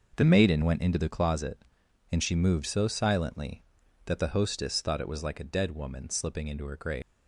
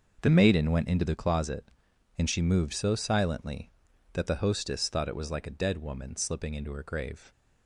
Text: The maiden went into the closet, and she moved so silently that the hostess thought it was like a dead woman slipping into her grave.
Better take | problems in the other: second | leaves "grave" unfinished; at 7.0 s; 220 ms

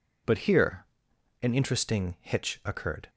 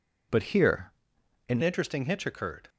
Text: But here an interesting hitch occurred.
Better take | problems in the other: first | pauses between "here" and "an"; noticeable; at 0.9 s; 0.56 s long; noticeable in the first // changes voice at "interesting"; from 1.6 s on; 1.0 s long

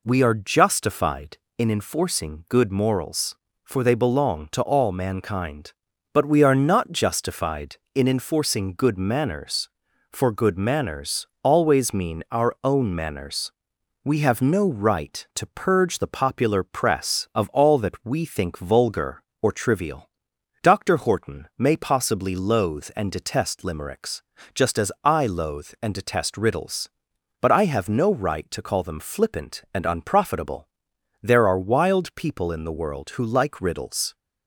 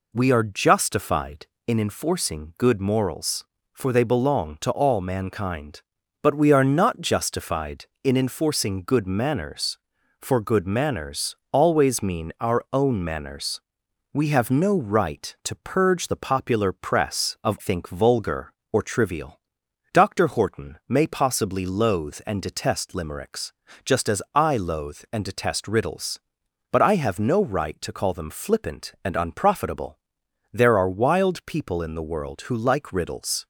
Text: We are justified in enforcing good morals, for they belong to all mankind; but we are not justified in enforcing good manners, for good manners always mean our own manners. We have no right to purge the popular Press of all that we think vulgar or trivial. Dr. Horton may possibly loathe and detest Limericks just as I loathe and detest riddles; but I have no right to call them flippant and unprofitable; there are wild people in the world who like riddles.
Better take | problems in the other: first | pauses between "manners" and "always"; slight; at 11.3 s; 0.16 s long; slight in the first // skips "all that we"; at 17.5 s // pauses between "Limericks" and "just"; slight; at 23.5 s; 0.34 s long; slight in the first

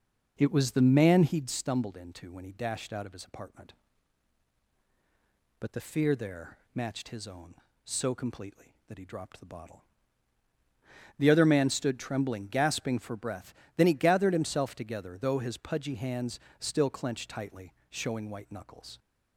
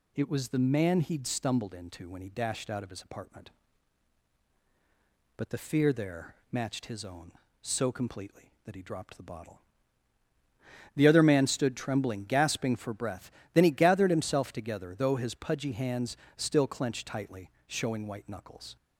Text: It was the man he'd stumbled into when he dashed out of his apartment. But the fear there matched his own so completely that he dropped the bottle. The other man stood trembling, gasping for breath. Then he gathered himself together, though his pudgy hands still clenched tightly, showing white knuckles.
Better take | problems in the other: second | starts louder than the rest; noticeable; until 1.5 s; 5.5 dB // pauses between "there" and "matched"; slight; at 6.5 s; 0.16 s long; slight in the second // pauses between "hands" and "still"; slight; at 16.3 s; 0.20 s long; slight in the second

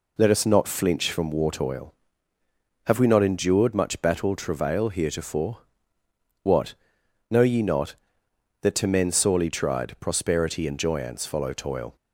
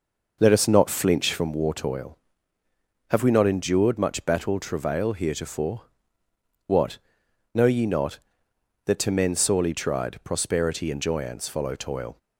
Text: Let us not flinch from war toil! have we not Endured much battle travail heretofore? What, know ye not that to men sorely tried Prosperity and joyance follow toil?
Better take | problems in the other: first | starts louder than the rest; noticeable; until 1.5 s; 5.5 dB

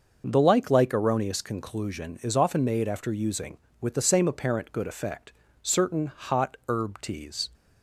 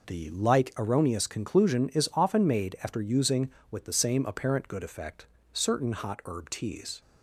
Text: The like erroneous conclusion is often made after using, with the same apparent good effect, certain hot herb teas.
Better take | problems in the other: second | starts louder than the rest; noticeable; until 1.2 s; 6 dB // says "like" twice; at 0.7 s

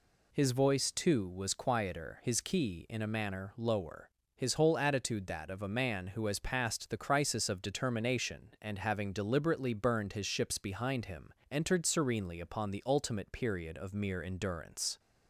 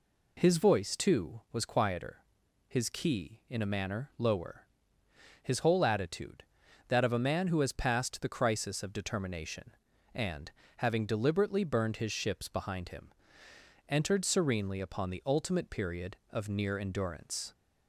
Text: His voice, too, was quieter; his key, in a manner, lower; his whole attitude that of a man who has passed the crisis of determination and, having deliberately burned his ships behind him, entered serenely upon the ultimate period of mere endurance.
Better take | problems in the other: first | says "near" for "mere"; at 16.4 s

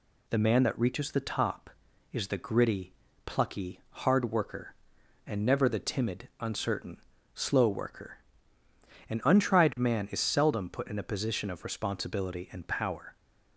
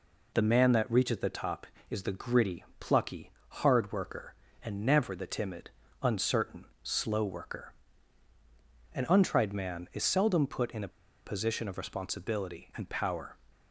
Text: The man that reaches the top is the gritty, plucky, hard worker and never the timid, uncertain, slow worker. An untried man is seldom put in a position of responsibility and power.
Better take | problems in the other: first | pauses between "a" and "position"; at 10.8 s; 0.36 s long

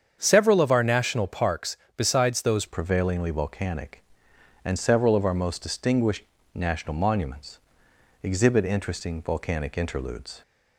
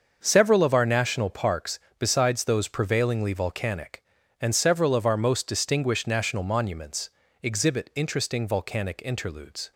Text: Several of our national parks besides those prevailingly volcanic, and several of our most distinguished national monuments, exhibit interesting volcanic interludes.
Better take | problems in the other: second | starts louder than the rest; strong; until 1.2 s; 7.5 dB; also in the second // pauses between "parks" and "besides"; slight; at 1.7 s; 0.18 s long; slight in the second // changes voice at "prevailingly"; from 2.6 s on; 7.8 s long // pauses between "distinguished" and "national"; slight; at 6.2 s; 0.32 s long

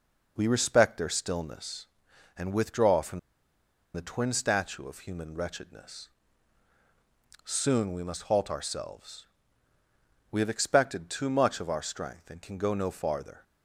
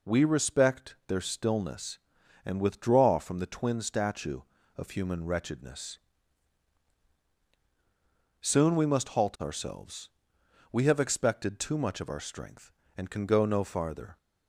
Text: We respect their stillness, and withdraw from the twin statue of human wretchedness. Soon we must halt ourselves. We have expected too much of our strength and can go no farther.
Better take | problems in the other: second | pauses between "from" and "the"; noticeable; at 3.1 s; 0.75 s long

